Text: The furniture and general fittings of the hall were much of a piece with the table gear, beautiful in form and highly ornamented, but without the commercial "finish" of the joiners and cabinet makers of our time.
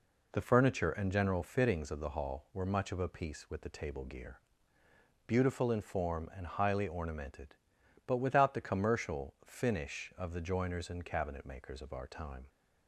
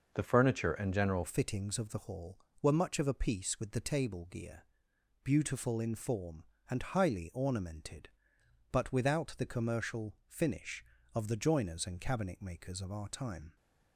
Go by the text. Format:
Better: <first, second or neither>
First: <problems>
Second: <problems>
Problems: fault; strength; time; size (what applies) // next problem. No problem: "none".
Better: first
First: none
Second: changes voice at "fittings"; from 1.2 s on; 12.3 s long